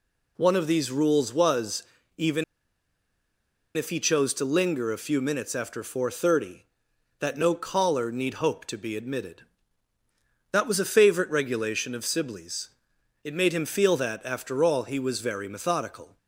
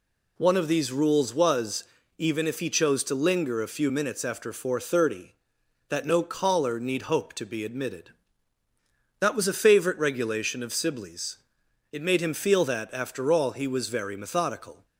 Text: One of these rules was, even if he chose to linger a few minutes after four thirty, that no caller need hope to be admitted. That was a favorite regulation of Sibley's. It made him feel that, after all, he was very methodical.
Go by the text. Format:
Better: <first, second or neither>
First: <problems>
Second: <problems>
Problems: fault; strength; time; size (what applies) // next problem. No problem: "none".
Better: second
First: pauses between "even" and "if"; strong; at 2.4 s; 1.3 s long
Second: none